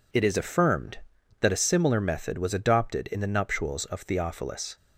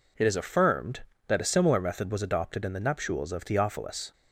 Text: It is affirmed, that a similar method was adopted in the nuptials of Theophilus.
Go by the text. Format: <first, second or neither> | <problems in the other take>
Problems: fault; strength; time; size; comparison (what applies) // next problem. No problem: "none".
neither | none